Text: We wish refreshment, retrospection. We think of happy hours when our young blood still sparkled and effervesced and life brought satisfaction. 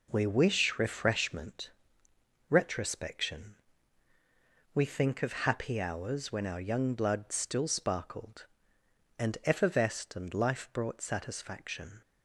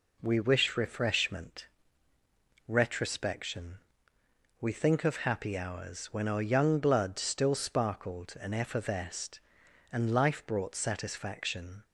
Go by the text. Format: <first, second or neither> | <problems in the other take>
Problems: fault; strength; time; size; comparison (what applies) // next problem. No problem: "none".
neither | none